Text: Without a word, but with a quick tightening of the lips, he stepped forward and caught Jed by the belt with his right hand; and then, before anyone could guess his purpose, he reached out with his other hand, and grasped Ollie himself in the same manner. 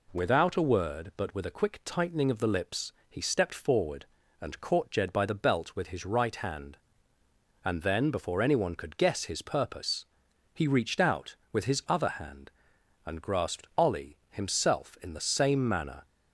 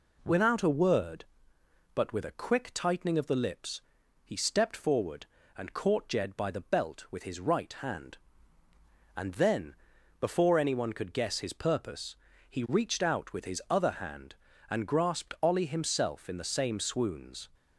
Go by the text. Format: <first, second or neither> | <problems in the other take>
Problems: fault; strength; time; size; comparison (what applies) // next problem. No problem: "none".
first | says "swoons" for "manner"; at 16.7 s